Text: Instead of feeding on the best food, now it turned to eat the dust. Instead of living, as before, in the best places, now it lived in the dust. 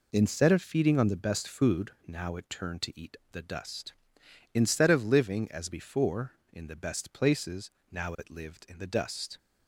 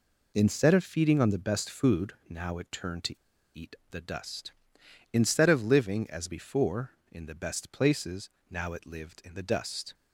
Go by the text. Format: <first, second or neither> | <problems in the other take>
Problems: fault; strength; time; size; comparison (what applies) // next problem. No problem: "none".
first | pauses between "to" and "eat"; at 3.1 s; 0.39 s long // pauses between "eat" and "the"; slight; at 3.7 s; 0.18 s long; slight in the first